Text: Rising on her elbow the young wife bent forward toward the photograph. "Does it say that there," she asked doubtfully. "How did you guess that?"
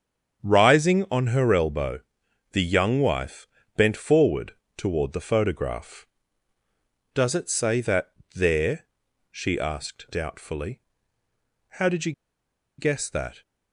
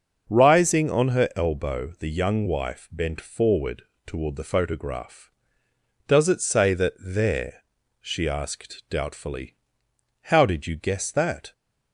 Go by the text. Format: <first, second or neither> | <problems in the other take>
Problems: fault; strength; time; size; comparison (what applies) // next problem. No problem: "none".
second | starts louder than the rest; strong; until 1.5 s; 7.5 dB; also in the second // pauses between "elbow" and "the"; noticeable; at 1.9 s; 0.52 s long // pauses between "wife" and "bent"; slight; at 3.4 s; 0.30 s long // pauses between "forward" and "toward"; slight; at 4.5 s; 0.24 s long; slight in the second // pauses between "that" and "there"; slight; at 8.1 s; 0.22 s long // pauses between "you" and "guess"; noticeable; at 12.1 s; 0.66 s long